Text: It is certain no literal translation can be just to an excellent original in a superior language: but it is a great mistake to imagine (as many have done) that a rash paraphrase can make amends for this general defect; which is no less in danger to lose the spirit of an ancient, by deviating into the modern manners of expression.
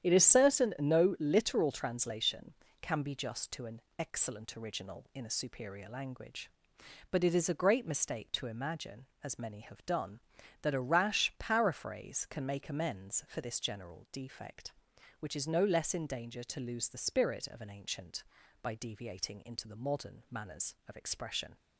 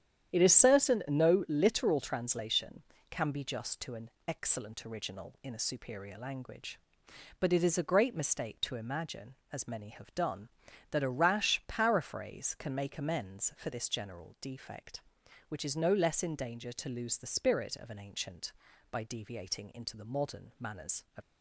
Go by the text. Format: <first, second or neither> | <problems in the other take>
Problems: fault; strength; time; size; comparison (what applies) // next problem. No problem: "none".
first | starts louder than the rest; strong; until 1.3 s; 10 dB; strong in the first // pauses between "an" and "excellent"; slight; at 4.1 s; 0.16 s long; slight in the first // stops before "expression"; at 21.2 s